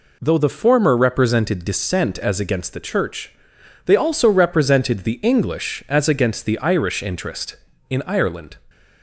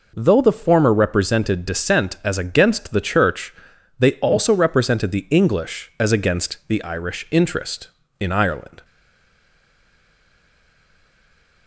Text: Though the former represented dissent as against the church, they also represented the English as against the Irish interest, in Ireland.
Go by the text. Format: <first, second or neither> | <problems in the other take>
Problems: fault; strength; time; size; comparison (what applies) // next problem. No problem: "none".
first | stays silent after the last word; strong; from 8.8 s on; 2.8 s long